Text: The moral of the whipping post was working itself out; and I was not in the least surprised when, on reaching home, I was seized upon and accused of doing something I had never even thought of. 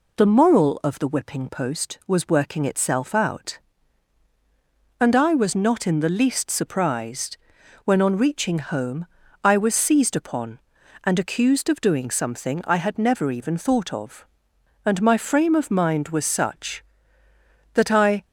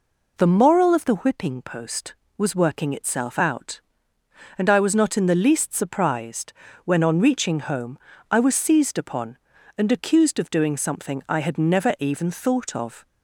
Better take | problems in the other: second | pauses between "surprised" and "when"; noticeable; at 7.3 s; 0.48 s long; slight in the second // goes on to say "And my frame of mind was such that I"; strong; from 14.8 s on; 3.4 s long

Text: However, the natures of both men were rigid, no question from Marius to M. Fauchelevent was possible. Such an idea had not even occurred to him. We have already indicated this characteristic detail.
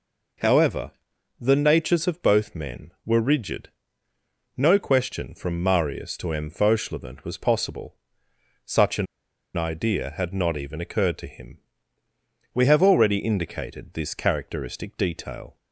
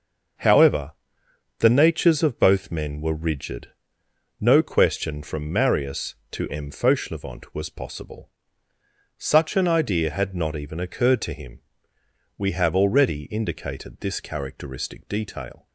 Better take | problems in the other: second | pauses between "an" and "idea"; noticeable; at 9.0 s; 0.49 s long

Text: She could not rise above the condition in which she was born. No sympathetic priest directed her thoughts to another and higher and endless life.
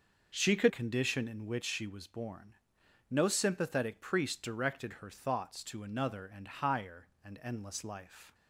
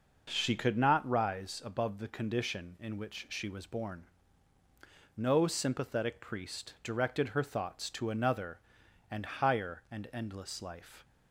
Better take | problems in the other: second | skips "not rise above the"; at 0.6 s

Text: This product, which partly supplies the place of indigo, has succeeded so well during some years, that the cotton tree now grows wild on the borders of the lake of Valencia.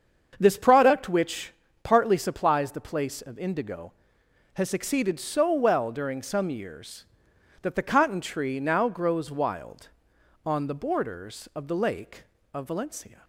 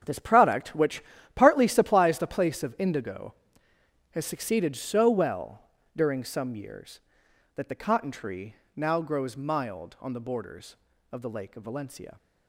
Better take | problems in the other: first | starts louder than the rest; strong; until 1.3 s; 7.5 dB; strong in the first // pauses between "which" and "partly"; slight; at 1.0 s; 0.34 s long; slight in the first // pauses between "well" and "during"; slight; at 5.6 s; 0.34 s long // pauses between "tree" and "now"; slight; at 8.5 s; 0.20 s long // says "mild" for "wild"; at 9.3 s

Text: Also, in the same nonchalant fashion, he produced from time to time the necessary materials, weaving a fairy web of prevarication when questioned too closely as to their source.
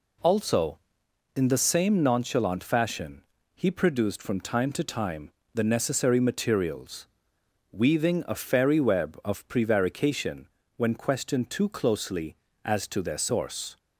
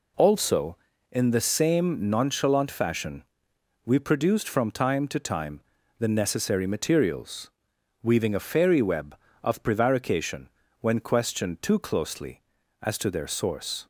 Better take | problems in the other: first | says "we" for "he"; at 3.8 s // pauses between "time" and "the"; at 5.6 s; 0.38 s long; slight in the first // pauses between "prevarication" and "when"; slight; at 10.4 s; 0.32 s long; slight in the first

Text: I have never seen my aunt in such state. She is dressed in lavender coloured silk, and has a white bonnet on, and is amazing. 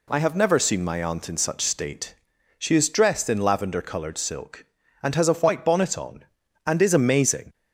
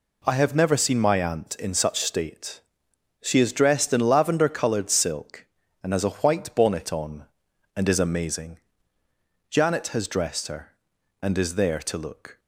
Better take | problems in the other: first | goes on to say "Janet has dressed her and is there to look"; strong; from 9.4 s on; 2.9 s long

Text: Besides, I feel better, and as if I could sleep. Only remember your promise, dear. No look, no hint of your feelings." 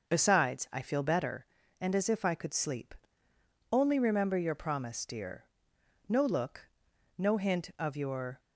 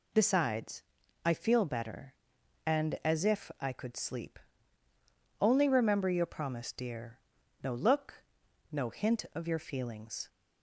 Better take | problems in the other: second | stops before "feelings"; at 8.3 s

